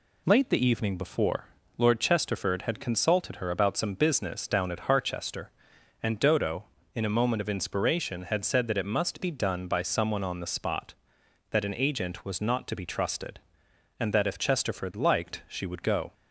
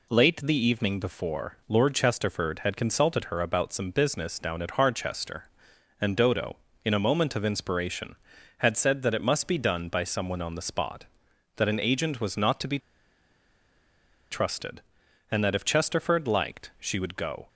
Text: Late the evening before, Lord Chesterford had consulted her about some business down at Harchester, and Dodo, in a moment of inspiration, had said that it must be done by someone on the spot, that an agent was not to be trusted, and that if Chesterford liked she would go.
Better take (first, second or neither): first